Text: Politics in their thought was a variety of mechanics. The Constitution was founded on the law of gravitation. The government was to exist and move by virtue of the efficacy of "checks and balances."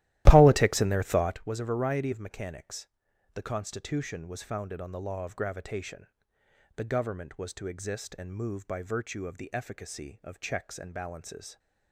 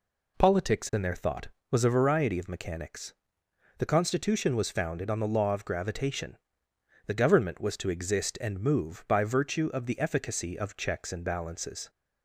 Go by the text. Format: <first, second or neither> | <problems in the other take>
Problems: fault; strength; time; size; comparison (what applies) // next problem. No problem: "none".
second | starts louder than the rest; strong; until 1.5 s; 14.5 dB